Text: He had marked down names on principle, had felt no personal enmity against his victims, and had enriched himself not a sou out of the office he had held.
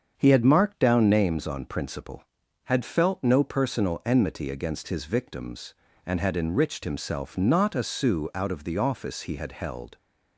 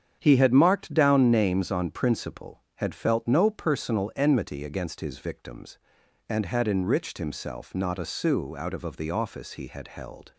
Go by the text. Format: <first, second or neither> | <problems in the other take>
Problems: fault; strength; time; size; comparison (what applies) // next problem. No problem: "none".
first | starts louder than the rest; strong; until 1.2 s; 8 dB; also in the first // says "of" twice; at 8.8 s